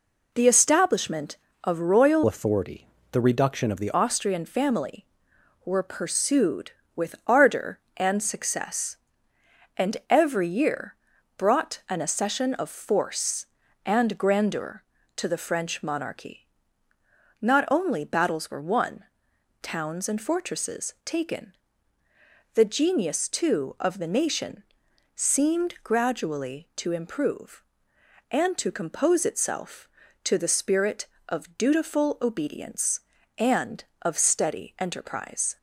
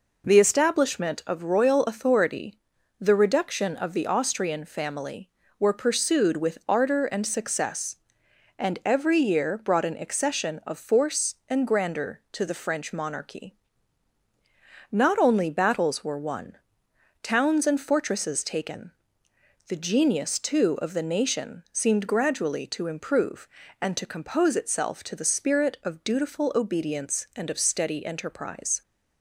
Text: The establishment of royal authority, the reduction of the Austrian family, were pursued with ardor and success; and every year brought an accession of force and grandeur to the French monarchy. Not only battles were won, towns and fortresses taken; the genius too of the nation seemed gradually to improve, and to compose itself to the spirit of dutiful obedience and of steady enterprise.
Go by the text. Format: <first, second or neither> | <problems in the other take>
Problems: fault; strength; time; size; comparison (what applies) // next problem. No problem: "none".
second | changes voice from "authority" to "the"; from 2.2 to 3.9 s; 1.7 s long // pauses between "year" and "brought"; at 10.9 s; 0.42 s long // pauses between "nation" and "seemed"; noticeable; at 24.6 s; 0.54 s long